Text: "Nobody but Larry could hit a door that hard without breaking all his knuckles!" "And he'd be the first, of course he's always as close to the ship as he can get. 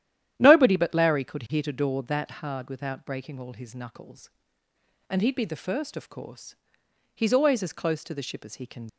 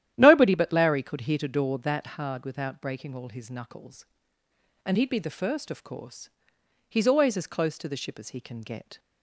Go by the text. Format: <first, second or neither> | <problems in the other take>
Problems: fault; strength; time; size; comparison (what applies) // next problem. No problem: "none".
second | starts louder than the rest; strong; until 1.3 s; 11 dB; strong in the second // pauses between "course" and "he's"; noticeable; at 6.5 s; 0.58 s long; noticeable in the second // stops before "get"; at 8.8 s